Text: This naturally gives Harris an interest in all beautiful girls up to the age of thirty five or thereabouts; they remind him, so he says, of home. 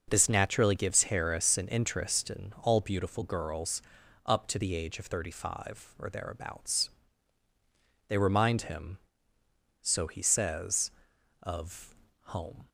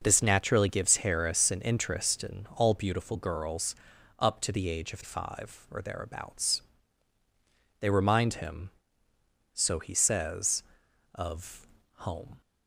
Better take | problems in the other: first | pauses between "girls" and "up"; at 3.7 s; 0.44 s long; also in the first // skips "thirty"; at 5.0 s // pauses between "of" and "home"; slight; at 11.6 s; 0.28 s long; slight in the first

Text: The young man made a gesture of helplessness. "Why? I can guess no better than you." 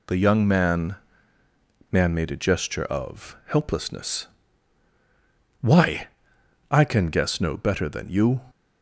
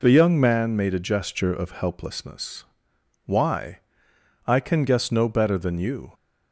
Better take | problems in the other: second | says "man" twice; at 1.9 s

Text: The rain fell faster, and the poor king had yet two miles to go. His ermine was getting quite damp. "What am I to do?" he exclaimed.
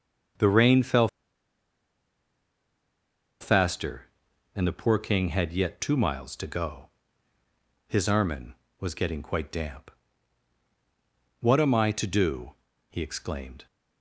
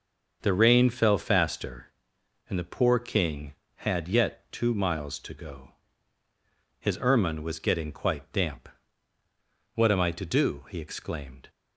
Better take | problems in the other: second | starts louder than the rest; strong; until 3.7 s; 7.5 dB; also in the second // pauses between "fell" and "faster"; strong; at 1.0 s; 2.3 s long

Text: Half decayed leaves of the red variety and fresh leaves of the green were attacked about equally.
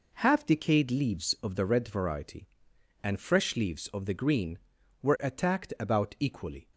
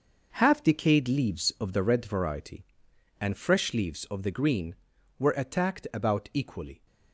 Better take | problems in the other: first | gets quieter; strong; throughout; 9 dB

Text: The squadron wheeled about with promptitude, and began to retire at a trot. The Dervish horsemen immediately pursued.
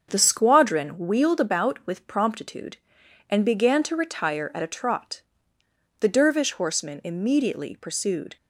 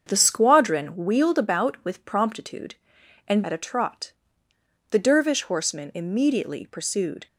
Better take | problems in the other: first | starts louder than the rest; until 1.0 s; 7 dB; also in the first // skips "began to retire"; at 3.4 s

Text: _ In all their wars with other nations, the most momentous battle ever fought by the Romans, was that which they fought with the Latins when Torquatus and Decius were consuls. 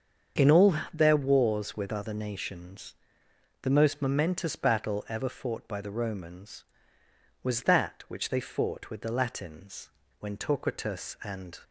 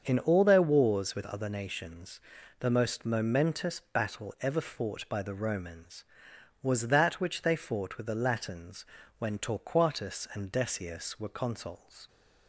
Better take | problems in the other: second | starts louder than the rest; strong; until 1.5 s; 7.5 dB; also in the second // pauses between "all" and "their"; slight; at 0.7 s; 0.18 s long // pauses between "Latins" and "when"; slight; at 9.8 s; 0.31 s long; slight in the second // stops before "Decius were consuls"; at 11.6 s

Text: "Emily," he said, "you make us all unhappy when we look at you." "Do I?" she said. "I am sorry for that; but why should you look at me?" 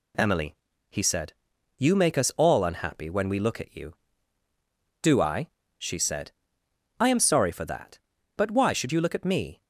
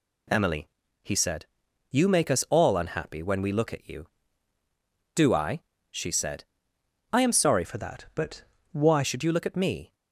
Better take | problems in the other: first | changes voice from "for" to "why"; from 7.6 to 9.0 s; 1.4 s long // pauses between "but" and "why"; slight; at 8.4 s; 0.30 s long

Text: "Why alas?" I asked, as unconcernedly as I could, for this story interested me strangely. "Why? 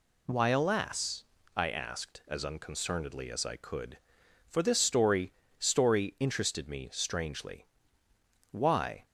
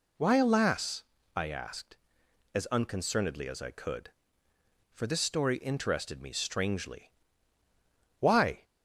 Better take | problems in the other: second | says "story" twice; at 5.5 s

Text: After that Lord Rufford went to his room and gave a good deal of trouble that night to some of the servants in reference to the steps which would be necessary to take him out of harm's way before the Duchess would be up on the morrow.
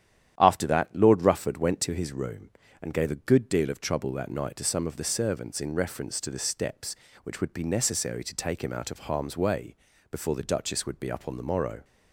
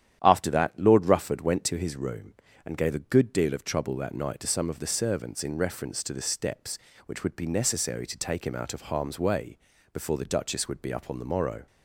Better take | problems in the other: neither | starts louder than the rest; strong; the same in both // pauses between "way" and "before"; slight; the same in both

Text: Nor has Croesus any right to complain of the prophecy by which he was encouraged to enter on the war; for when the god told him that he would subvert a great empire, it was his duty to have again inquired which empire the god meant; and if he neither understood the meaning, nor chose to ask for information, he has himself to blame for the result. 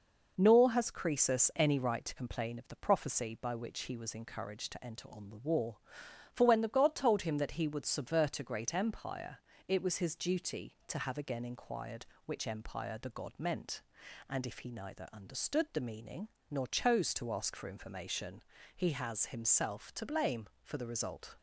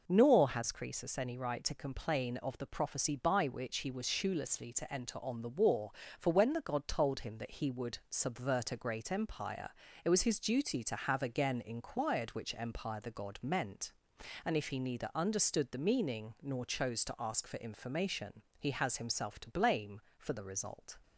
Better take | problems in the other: first | says "shoelessly" for "encouraged"; at 4.0 s

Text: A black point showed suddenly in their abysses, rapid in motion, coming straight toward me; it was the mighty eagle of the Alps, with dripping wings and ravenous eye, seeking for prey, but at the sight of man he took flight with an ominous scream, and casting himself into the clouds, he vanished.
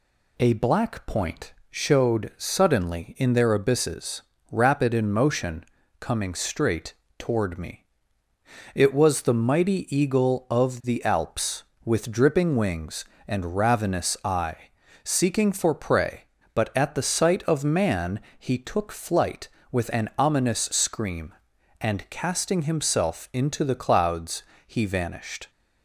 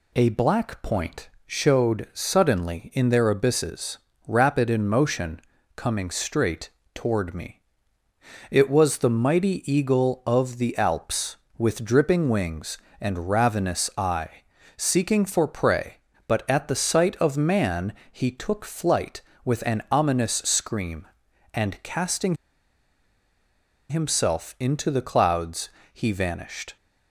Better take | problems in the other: first | pauses between "point" and "showed"; slight; at 1.2 s; 0.18 s long; slight in the first // pauses between "straight" and "toward"; slight; at 6.6 s; 0.24 s long; slight in the first // pauses between "man" and "he"; slight; at 17.9 s; 0.20 s long; slight in the first // pauses between "casting" and "himself"; strong; at 22.3 s; 1.5 s long

